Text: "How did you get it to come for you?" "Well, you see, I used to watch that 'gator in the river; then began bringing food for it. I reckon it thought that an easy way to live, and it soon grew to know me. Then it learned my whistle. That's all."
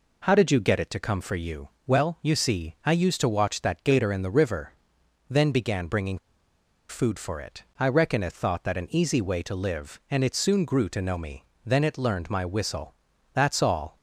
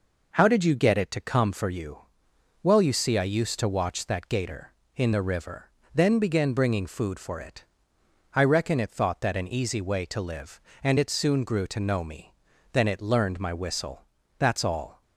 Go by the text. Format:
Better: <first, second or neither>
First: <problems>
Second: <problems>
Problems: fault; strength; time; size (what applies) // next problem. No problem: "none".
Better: second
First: pauses between "bringing" and "food"; noticeable; at 6.1 s; 0.72 s long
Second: none